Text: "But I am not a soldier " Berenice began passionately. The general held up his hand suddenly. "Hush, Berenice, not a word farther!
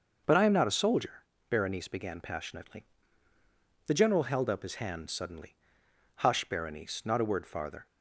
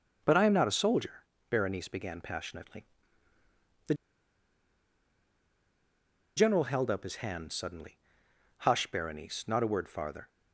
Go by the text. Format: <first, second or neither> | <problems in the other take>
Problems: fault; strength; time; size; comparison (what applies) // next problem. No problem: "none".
first | pauses between "The" and "general"; strong; at 3.9 s; 2.4 s long